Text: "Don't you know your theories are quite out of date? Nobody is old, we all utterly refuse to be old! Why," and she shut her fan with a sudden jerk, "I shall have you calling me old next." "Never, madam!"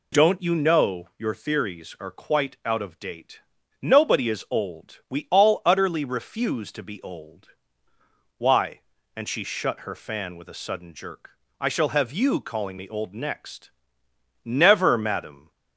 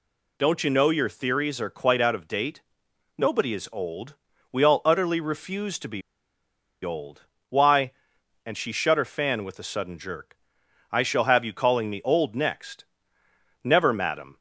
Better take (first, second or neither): first